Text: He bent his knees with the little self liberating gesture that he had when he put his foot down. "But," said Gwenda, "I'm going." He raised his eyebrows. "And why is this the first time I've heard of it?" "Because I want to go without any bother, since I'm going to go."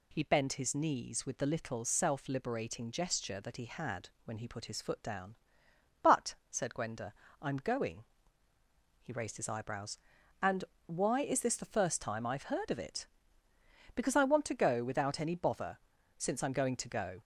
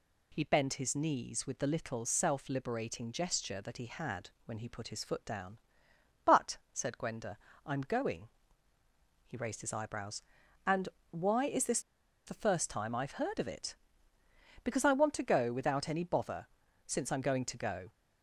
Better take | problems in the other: first | pauses between "had" and "when"; slight; at 4.3 s; 0.16 s long; slight in the first // pauses between "And" and "why"; slight; at 10.8 s; 0.22 s long; slight in the first // pauses between "this" and "the"; at 11.8 s; 0.45 s long

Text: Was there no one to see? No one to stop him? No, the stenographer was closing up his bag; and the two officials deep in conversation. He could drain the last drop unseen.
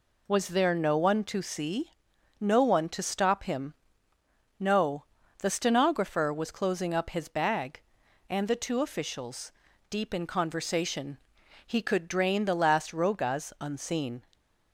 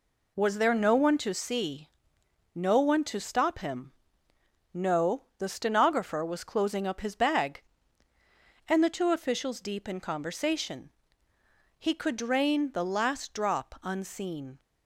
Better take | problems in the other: second | pauses between "officials" and "deep"; at 9.5 s; 0.38 s long // says "rogas" for "drop"; at 12.9 s

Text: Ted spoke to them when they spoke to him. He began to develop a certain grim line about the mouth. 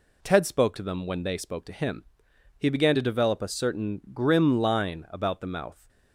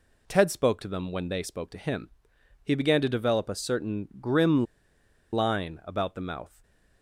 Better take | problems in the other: first | pauses between "grim" and "line"; noticeable; at 4.6 s; 0.68 s long // stays silent after the last word; slight; from 6.4 s on; 0.6 s long

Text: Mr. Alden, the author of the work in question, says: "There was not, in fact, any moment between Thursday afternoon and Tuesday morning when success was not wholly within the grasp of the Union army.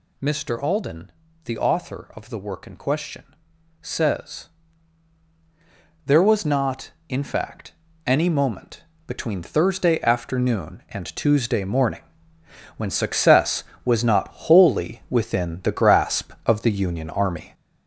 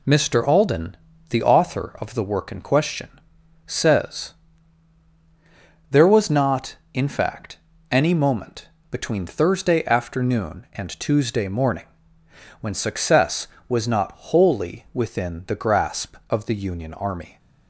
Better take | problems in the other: second | gets louder; noticeable; throughout; 5.5 dB // pauses between "moment" and "between"; slight; at 8.8 s; 0.25 s long; slight in the second // pauses between "morning" and "when"; noticeable; at 12.0 s; 0.78 s long; noticeable in the second // pauses between "not" and "wholly"; slight; at 14.2 s; 0.18 s long; slight in the second

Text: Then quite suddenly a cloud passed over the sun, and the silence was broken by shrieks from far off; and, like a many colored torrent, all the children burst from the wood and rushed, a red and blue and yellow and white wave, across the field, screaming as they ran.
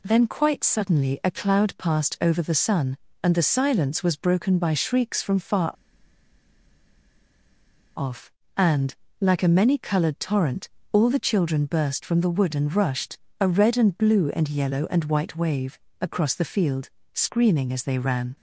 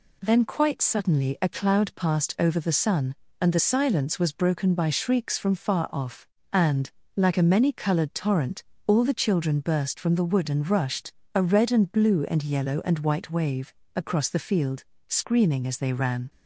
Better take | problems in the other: second | pauses between "far" and "off"; strong; at 5.7 s; 2.2 s long

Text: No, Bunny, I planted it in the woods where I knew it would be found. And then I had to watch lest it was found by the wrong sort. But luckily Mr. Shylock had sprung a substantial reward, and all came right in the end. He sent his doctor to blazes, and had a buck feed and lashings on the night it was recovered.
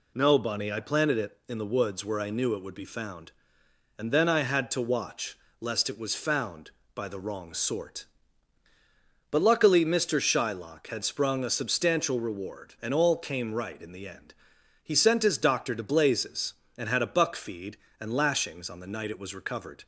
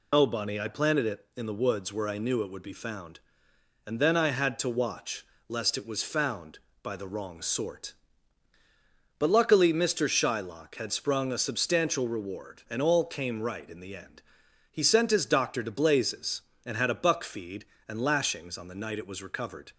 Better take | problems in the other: first | loses the start of "No"; at 0.1 s; 95 ms // pauses between "watch" and "lest"; slight; at 5.2 s; 0.22 s long; slight in the first

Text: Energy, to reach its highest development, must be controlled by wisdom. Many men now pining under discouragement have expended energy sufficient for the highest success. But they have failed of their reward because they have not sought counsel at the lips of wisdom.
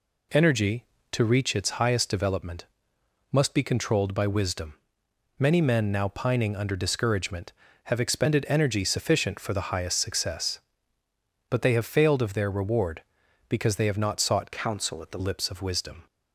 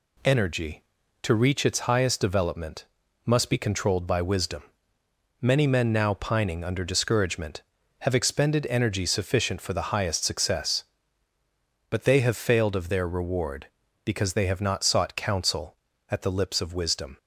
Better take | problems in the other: second | changes voice from "counsel" to "the"; from 14.5 to 15.1 s; 0.6 s long

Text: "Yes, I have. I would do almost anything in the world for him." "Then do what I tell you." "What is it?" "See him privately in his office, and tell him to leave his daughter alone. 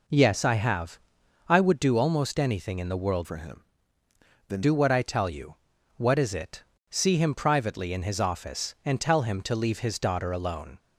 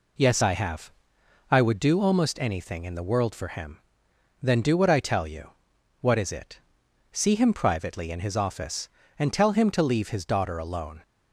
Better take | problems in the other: second | changes voice from "for" to "Then"; from 3.2 to 4.6 s; 1.4 s long

